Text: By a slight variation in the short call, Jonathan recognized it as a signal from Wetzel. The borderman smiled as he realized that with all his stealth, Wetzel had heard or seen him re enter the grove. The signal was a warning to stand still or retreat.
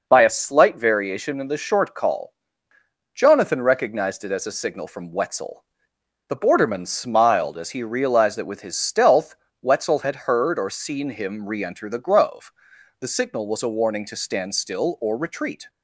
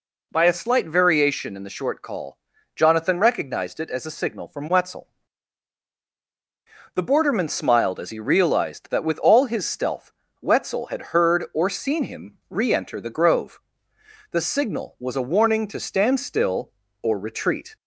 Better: second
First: skips "all"; at 8.6 s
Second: none

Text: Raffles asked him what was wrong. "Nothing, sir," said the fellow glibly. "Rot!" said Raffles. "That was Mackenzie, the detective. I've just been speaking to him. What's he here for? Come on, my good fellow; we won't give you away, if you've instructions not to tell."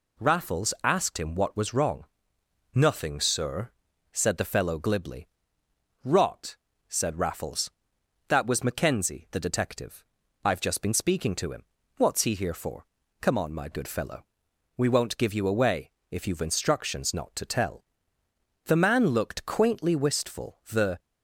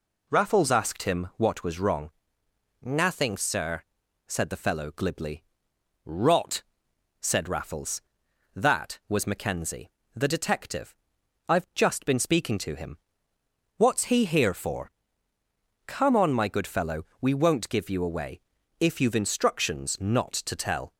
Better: second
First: goes on to say "The man looked quaintly wistful the"; strong; from 18.6 s on; 2.3 s long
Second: none

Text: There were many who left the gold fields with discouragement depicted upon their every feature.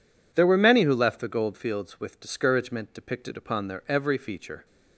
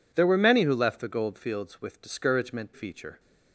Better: first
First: none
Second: skips "depicted upon their every"; at 2.7 s

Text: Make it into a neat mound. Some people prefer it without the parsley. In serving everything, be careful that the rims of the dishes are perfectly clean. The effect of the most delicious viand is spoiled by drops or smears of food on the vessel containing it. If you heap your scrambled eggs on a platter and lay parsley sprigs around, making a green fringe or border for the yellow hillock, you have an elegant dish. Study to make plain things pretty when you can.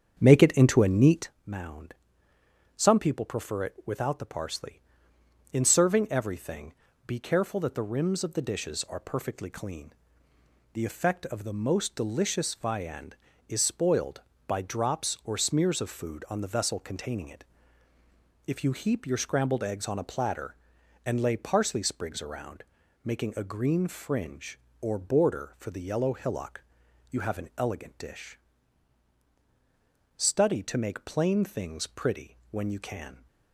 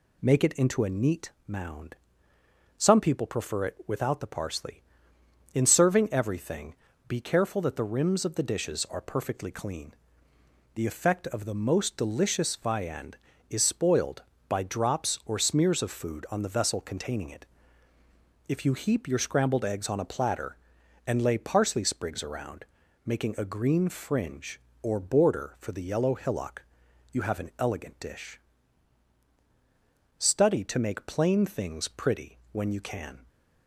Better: second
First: starts louder than the rest; strong; until 1.3 s; 7.5 dB // pauses between "neat" and "mound"; slight; at 1.2 s; 0.16 s long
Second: pauses between "neat" and "mound"; slight; at 1.3 s; 0.16 s long

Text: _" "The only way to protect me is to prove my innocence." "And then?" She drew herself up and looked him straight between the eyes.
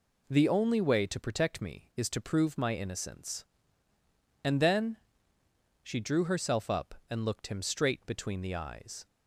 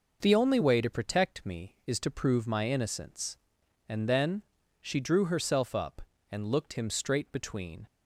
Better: first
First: none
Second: stops before "the eyes"; at 7.8 s

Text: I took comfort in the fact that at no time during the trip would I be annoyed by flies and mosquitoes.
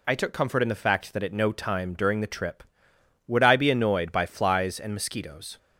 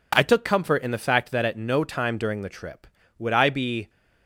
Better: first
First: none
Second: stops before "annoyed by flies and mosquitoes"; at 3.8 s

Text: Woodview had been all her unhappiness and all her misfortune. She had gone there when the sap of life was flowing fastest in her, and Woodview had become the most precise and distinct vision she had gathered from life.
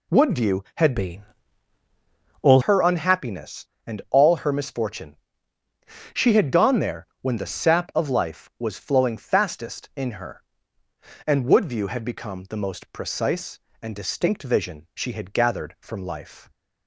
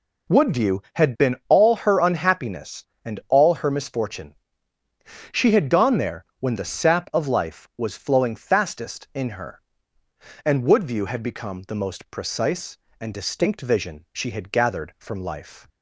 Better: second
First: changes voice from "been" to "all"; from 0.9 to 2.6 s; 1.7 s long // pauses between "been" and "all"; at 1.2 s; 1.2 s long // pauses between "there" and "when"; slight; at 7.0 s; 0.16 s long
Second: pauses between "there" and "when"; slight; at 6.2 s; 0.16 s long

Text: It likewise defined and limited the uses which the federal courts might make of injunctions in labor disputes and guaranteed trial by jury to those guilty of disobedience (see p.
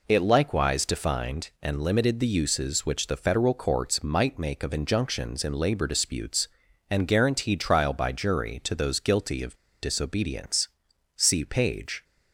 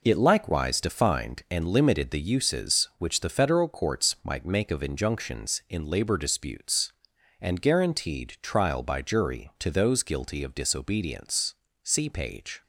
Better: second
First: pauses between "of" and "disobedience"; slight; at 9.5 s; 0.25 s long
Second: none

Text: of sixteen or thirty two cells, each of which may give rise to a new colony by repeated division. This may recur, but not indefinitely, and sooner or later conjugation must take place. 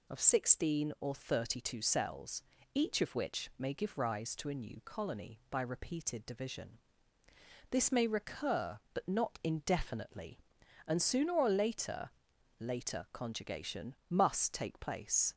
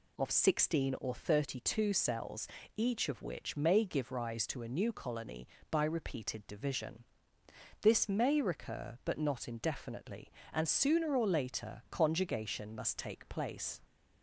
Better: second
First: says "later" twice; at 12.5 s // pauses between "conjugation" and "must"; slight; at 13.9 s; 0.16 s long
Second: none

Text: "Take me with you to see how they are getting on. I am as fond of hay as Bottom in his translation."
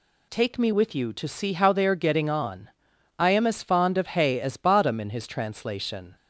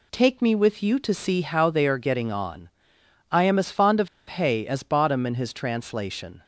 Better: first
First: none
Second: pauses between "of" and "hay"; slight; at 4.0 s; 0.20 s long

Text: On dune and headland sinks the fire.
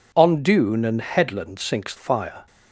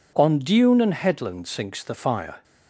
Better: second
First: skips "the"; at 1.9 s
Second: none

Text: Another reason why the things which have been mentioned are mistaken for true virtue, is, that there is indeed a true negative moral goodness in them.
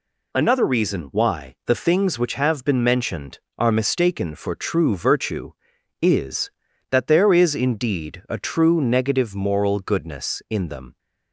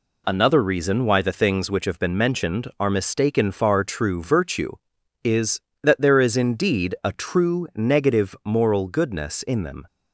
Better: first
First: none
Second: says "far" for "for"; at 3.5 s

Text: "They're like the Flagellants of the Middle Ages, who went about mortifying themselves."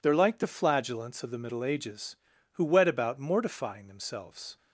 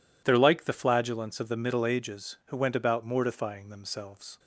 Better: second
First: says "wet" for "went"; at 2.6 s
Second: none

